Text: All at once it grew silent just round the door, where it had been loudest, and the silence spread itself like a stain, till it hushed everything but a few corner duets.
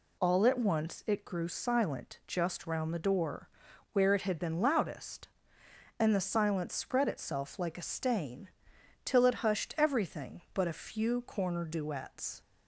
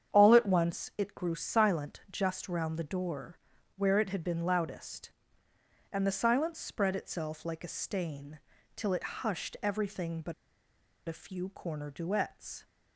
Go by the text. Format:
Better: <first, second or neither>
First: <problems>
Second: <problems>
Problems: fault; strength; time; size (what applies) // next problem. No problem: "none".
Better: first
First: none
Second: starts louder than the rest; strong; until 1.2 s; 8.5 dB // pauses between "but" and "a"; noticeable; at 10.3 s; 0.74 s long